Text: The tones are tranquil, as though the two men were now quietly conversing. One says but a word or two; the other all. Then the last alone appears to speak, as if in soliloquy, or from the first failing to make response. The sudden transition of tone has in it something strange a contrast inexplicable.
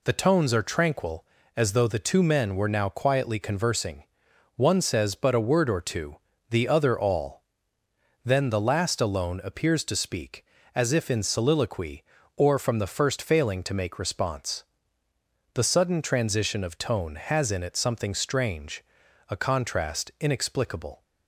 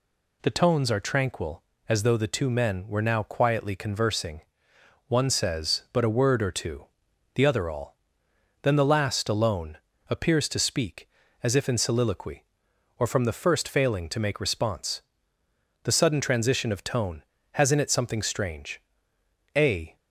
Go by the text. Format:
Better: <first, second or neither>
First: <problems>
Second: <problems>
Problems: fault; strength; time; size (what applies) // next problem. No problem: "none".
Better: first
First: pauses between "strange" and "a"; noticeable; at 18.8 s; 0.46 s long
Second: pauses between "alone" and "appears"; slight; at 9.7 s; 0.34 s long // pauses between "strange" and "a"; noticeable; at 18.7 s; 0.76 s long // stops before "contrast inexplicable"; at 19.9 s